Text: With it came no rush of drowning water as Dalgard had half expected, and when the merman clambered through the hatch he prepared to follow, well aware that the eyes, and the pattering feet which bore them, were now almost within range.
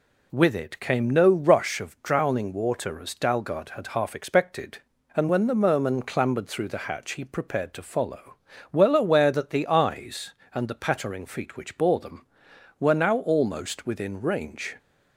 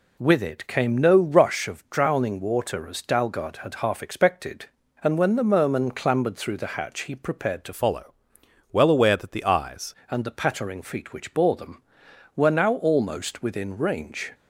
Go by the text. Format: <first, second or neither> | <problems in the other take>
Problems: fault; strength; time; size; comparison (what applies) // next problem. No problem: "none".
first | changes voice from "follow" to "eyes"; from 7.7 to 9.9 s; 2.2 s long